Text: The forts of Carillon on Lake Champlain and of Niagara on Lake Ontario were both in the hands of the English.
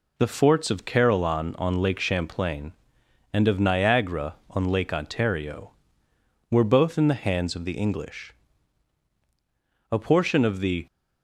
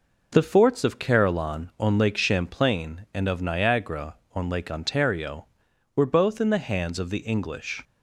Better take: second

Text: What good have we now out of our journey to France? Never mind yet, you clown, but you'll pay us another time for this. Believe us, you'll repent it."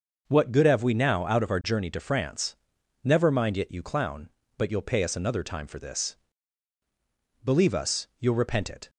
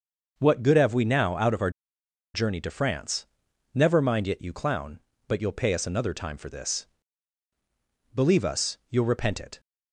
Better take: first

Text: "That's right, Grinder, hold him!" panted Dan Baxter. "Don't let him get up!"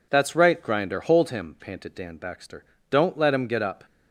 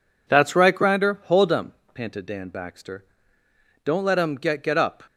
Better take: first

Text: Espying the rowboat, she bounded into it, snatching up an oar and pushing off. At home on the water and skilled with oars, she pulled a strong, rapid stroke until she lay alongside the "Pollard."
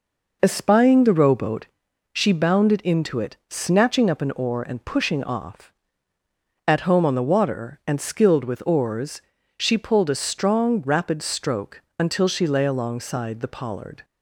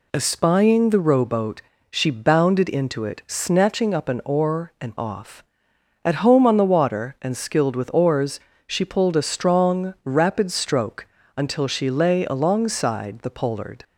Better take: first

